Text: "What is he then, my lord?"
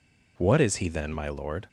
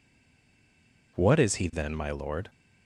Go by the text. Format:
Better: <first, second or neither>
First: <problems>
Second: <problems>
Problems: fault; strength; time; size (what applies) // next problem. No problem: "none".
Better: first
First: none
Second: stays silent before the first word; until 1.1 s; 1.1 s long